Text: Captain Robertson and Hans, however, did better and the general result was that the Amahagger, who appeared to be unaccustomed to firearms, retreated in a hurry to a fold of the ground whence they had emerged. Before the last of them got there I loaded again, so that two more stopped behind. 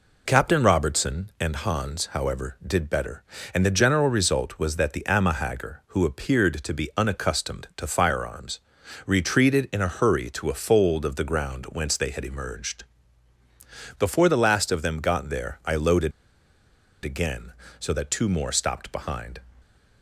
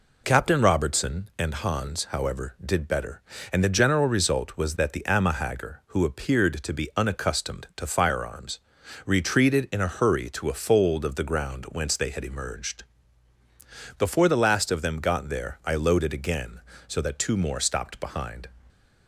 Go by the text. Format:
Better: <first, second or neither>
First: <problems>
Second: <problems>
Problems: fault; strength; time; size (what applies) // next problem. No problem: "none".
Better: second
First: pauses between "loaded" and "again"; noticeable; at 16.1 s; 0.93 s long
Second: none